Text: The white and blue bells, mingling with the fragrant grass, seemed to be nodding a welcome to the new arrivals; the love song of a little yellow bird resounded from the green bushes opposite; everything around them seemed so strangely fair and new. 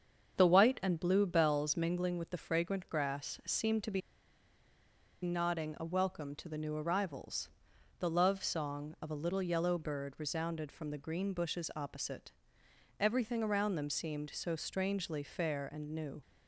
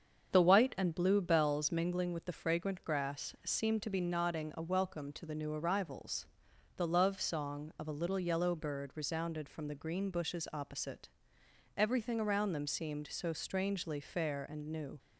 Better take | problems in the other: second | starts louder than the rest; strong; until 1.4 s; 7.5 dB; strong in the second // pauses between "be" and "nodding"; at 4.0 s; 1.2 s long

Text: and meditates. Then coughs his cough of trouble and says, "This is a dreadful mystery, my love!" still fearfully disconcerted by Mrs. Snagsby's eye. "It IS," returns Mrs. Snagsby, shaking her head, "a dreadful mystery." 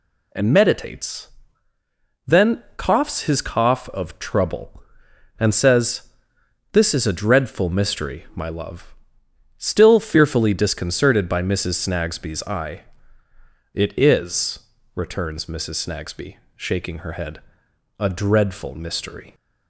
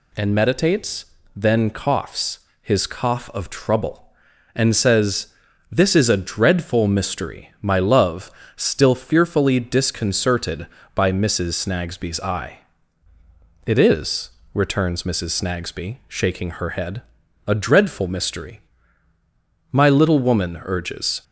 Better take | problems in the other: first | pauses between "coughs" and "his"; slight; at 2.3 s; 0.22 s long // goes on to say "My little woman urges"; from 19.7 s on; 1.5 s long

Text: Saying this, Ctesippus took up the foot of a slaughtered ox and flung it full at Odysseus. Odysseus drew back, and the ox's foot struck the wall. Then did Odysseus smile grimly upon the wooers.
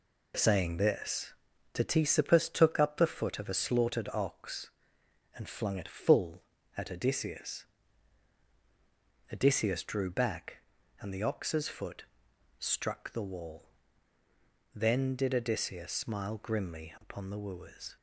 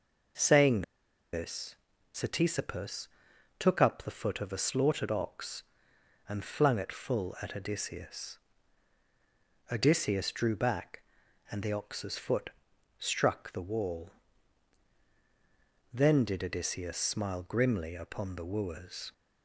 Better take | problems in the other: first | pauses between "Saying" and "this"; noticeable; at 0.8 s; 0.50 s long // pauses between "Ctesippus" and "took"; noticeable; at 3.0 s; 0.50 s long // pauses between "foot" and "struck"; noticeable; at 12.5 s; 0.48 s long; noticeable in the first

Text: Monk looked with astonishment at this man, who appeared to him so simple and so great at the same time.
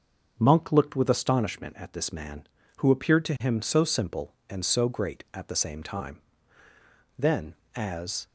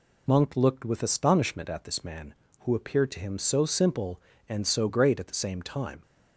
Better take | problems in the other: second | starts louder than the rest; until 1.3 s; 6.5 dB // goes on to say "Then as"; noticeable; from 7.1 s on; 1.1 s long

